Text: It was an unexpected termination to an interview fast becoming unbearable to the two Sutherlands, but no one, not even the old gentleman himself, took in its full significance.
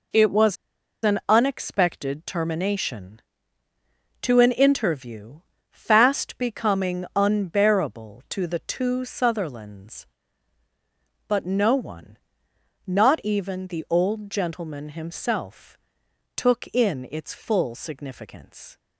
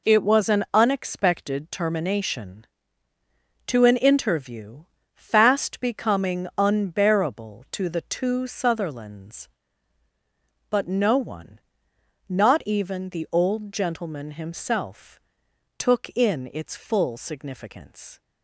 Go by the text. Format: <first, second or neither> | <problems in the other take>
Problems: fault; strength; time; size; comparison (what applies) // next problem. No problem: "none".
second | pauses between "was" and "an"; noticeable; at 0.5 s; 0.49 s long // pauses between "interview" and "fast"; slight; at 5.3 s; 0.32 s long; slight in the second